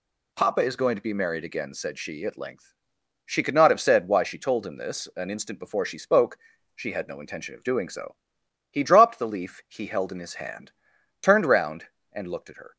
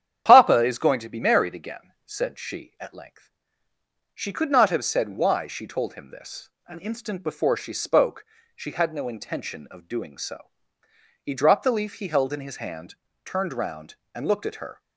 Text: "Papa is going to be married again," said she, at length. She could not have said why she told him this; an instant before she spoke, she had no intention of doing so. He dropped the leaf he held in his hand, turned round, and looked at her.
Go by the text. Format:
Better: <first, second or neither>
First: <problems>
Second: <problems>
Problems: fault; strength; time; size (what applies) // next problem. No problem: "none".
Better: first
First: none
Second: loses the start of "Papa"; at 0.2 s; 45 ms // starts louder than the rest; strong; until 1.2 s; 9.5 dB